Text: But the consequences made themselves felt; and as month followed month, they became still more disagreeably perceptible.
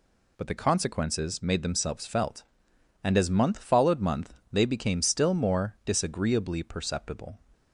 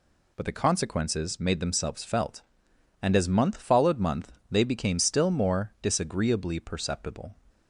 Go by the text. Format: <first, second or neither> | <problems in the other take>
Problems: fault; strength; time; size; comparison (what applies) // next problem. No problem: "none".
neither | none